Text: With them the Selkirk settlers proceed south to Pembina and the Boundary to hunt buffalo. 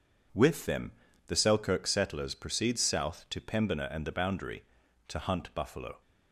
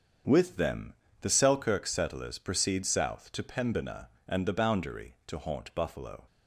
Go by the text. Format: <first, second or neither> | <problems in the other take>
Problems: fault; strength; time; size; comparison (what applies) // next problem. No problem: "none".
first | starts louder than the rest; until 1.5 s; 7 dB // pauses between "them" and "the"; slight; at 0.9 s; 0.28 s long; slight in the first // says "haunt" for "hunt"; at 5.3 s